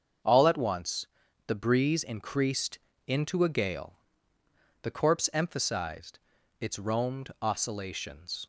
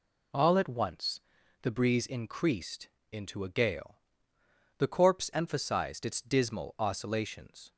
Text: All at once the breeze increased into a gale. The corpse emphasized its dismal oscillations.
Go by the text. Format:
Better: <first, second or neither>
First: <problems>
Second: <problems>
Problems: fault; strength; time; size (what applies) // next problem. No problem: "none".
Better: second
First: starts louder than the rest; until 1.6 s; 7 dB // pauses between "once" and "the"; at 1.0 s; 0.40 s long // pauses between "increased" and "into"; slight; at 2.7 s; 0.30 s long // pauses between "emphasized" and "its"; at 6.1 s; 0.40 s long // says "roamed" for "dismal"; at 6.7 s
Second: pauses between "once" and "the"; at 1.2 s; 0.42 s long // pauses between "increased" and "into"; slight; at 2.8 s; 0.22 s long